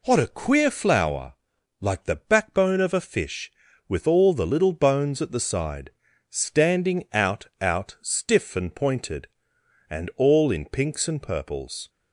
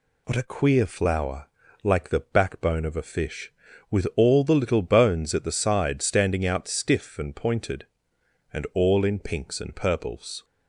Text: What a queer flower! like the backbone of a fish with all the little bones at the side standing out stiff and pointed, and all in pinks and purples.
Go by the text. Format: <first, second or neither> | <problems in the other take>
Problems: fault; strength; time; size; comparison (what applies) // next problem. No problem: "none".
second | pauses between "side" and "standing"; slight; at 5.9 s; 0.36 s long // says "out" twice; at 7.6 s